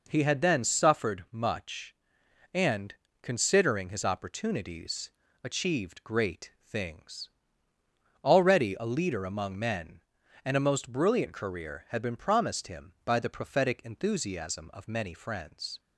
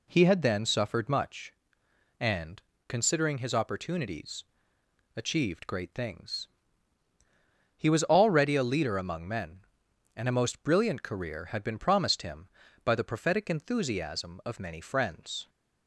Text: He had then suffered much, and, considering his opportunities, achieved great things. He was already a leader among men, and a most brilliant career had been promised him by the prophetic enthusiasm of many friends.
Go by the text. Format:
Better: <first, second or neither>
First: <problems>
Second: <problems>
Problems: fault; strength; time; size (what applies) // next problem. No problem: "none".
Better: second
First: skips "He was"; at 7.7 s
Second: none